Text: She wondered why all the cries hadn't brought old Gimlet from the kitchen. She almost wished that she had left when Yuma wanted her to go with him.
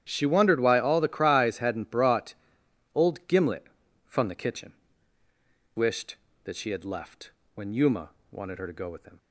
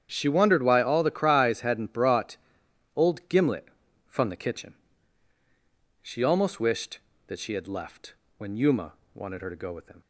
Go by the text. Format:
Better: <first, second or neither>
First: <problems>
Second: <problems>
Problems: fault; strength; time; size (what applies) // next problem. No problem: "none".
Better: second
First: starts louder than the rest; strong; until 1.1 s; 10 dB // pauses between "brought" and "old"; noticeable; at 2.3 s; 0.62 s long // skips "She almost"; at 5.2 s // pauses between "left" and "when"; slight; at 7.3 s; 0.24 s long // pauses between "Yuma" and "wanted"; slight; at 8.0 s; 0.20 s long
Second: starts louder than the rest; strong; until 1.1 s; 8.5 dB // pauses between "brought" and "old"; noticeable; at 2.3 s; 0.60 s long // pauses between "left" and "when"; slight; at 8.1 s; 0.24 s long // pauses between "Yuma" and "wanted"; slight; at 8.9 s; 0.20 s long